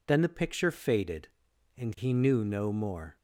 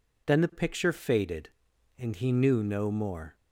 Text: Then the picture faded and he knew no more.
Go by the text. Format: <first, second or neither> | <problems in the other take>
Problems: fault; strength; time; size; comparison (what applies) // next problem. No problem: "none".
neither | none